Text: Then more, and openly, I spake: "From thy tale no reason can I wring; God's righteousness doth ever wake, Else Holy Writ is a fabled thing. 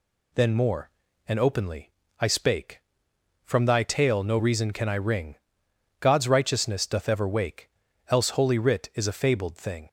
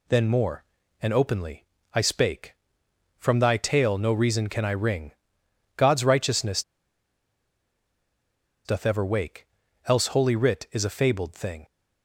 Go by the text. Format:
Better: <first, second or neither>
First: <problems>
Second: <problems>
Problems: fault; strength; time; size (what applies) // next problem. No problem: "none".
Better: first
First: none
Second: pauses between "righteousness" and "doth"; strong; at 6.6 s; 2.0 s long